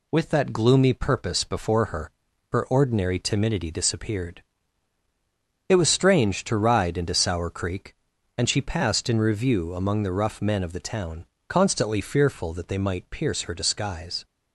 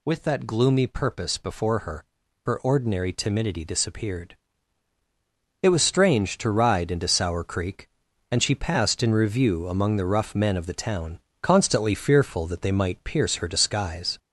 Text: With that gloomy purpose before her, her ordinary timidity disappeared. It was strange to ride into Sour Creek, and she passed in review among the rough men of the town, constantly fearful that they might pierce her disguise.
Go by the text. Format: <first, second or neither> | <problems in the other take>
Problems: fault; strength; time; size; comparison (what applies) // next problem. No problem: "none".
first | gets louder; slight; throughout; 2.5 dB